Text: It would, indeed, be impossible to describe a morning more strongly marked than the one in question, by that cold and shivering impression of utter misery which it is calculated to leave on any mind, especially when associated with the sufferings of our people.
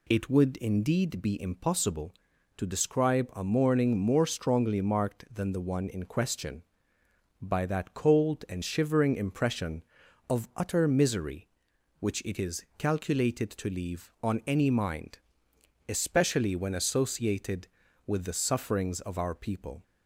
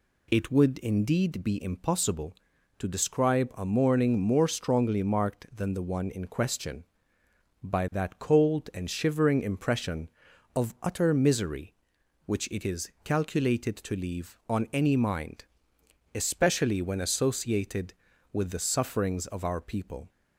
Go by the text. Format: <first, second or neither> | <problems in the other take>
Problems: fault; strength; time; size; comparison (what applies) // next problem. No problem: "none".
neither | none